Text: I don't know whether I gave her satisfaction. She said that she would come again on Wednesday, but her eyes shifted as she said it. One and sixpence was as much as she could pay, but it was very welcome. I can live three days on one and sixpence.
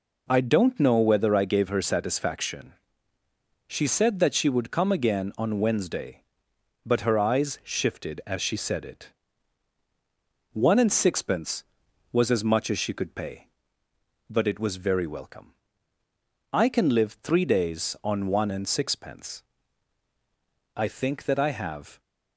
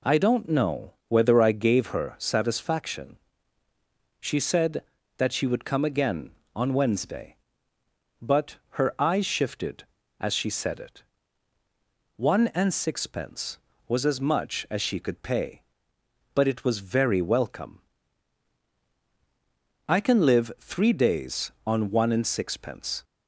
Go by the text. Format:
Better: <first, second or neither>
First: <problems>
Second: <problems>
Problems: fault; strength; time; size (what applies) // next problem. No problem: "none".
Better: second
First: goes on to say "I think that I have"; noticeable; from 20.7 s on; 1.2 s long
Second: none